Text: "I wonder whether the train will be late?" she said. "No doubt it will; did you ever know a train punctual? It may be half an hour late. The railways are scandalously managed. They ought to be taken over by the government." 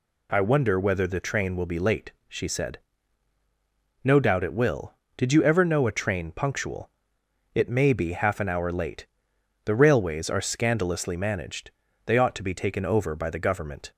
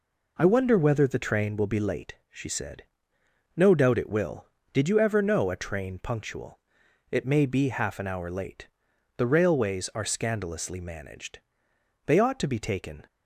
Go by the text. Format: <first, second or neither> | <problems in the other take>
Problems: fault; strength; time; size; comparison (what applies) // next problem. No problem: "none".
first | stops before "over by the government"; at 13.0 s